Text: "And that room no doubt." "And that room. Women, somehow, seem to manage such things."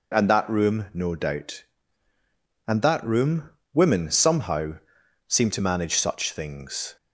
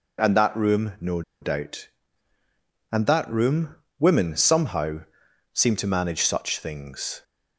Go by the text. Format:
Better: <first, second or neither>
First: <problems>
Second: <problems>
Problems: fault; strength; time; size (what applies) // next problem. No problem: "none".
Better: first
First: none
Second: pauses between "no" and "doubt"; slight; at 1.2 s; 0.20 s long